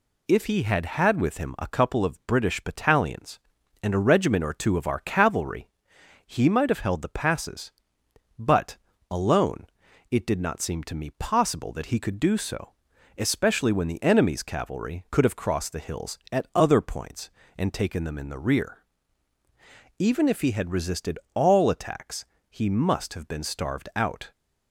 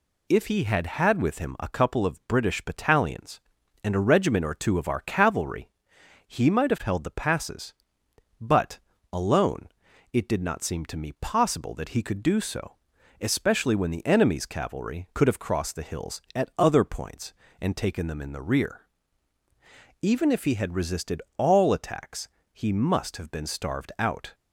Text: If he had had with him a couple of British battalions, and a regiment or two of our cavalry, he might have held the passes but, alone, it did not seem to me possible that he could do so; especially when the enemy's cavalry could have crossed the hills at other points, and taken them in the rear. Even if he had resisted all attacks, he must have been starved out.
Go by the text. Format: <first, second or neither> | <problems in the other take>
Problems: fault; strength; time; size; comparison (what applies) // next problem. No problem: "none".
neither | pauses between "resisted" and "all"; slight; the same in both